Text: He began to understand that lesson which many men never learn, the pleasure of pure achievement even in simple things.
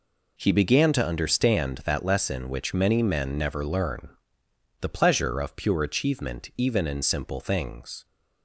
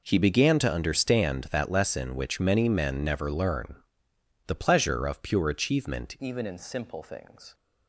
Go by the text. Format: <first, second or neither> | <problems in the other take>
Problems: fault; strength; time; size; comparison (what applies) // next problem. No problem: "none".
first | changes voice at "even"; from 6.1 s on; 1.4 s long